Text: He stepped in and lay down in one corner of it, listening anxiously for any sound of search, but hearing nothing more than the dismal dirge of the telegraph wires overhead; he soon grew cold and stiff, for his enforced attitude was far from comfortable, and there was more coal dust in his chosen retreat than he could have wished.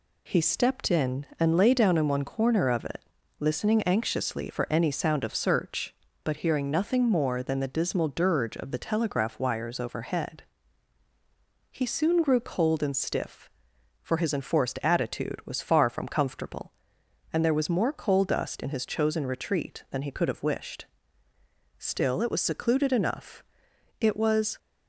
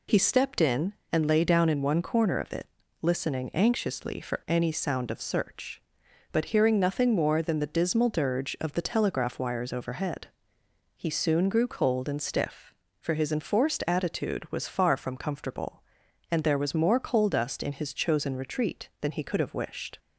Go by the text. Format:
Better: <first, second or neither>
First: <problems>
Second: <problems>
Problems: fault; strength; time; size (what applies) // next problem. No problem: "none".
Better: second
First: goes on to say "Still it was secluded enough it was"; strong; from 21.7 s on; 2.8 s long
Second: none